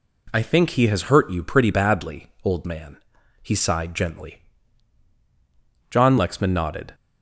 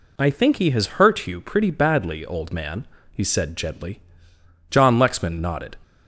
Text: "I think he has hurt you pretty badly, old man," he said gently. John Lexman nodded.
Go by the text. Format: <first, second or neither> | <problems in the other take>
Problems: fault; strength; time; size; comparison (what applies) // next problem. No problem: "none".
second | says "sighed" for "said"; at 3.5 s